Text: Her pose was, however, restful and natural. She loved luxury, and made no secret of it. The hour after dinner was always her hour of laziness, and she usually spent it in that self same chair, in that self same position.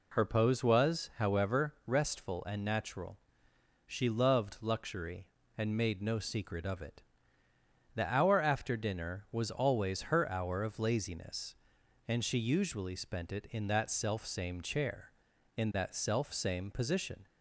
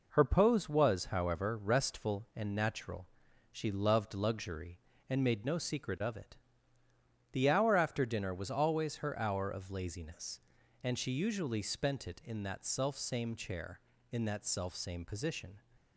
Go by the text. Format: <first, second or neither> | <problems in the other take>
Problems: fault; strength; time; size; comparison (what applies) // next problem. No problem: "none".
neither | none